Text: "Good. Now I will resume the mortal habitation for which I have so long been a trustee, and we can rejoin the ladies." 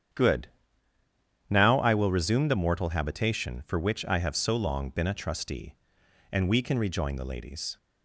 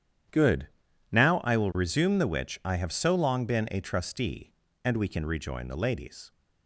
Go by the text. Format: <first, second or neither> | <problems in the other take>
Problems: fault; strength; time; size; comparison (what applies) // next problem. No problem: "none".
first | starts louder than the rest; strong; until 1.8 s; 9.5 dB; strong in the first // skips "mortal habitation for"; at 2.2 s